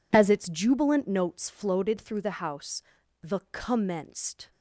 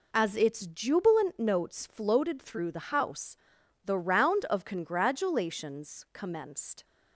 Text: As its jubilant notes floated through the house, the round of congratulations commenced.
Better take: second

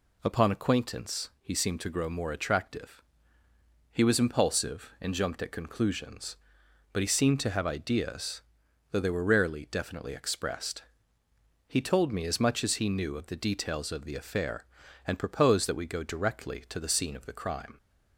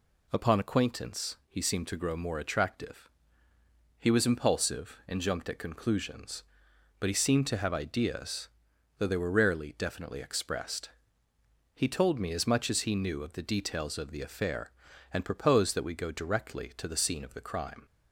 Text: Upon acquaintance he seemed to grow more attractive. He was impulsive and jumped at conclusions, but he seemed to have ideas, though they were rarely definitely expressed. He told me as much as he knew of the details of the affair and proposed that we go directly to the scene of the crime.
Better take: neither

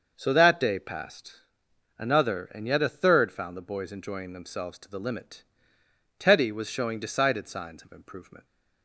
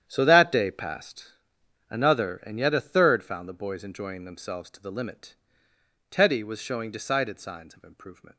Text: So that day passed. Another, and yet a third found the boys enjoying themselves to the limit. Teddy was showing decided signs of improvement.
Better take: first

